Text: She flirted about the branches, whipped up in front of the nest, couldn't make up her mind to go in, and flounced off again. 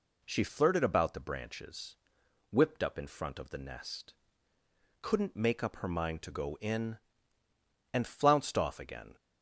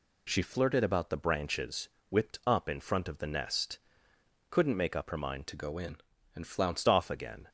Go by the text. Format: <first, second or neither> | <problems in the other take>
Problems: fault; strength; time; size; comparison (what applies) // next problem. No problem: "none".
first | changes voice from "to" to "flounced"; from 5.4 to 6.8 s; 1.4 s long